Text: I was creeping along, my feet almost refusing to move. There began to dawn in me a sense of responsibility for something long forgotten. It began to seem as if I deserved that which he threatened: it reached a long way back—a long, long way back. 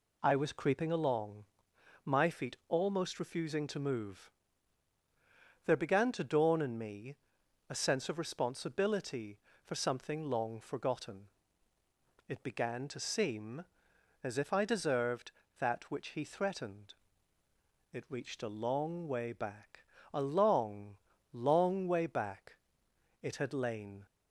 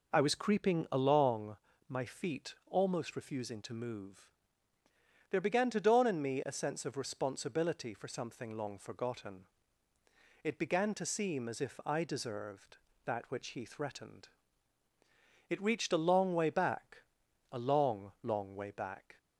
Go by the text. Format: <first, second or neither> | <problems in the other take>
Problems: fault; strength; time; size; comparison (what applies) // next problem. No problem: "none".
second | pauses between "me" and "a"; noticeable; at 7.1 s; 0.52 s long // goes on to say "It had lain"; noticeable; from 23.2 s on; 0.84 s long